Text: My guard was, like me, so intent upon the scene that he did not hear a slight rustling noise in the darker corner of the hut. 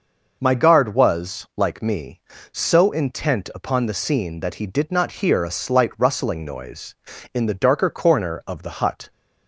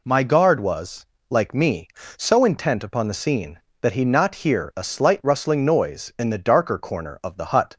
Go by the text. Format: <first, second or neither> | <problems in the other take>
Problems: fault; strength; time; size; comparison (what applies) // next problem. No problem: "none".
first | skips "did"; at 4.0 s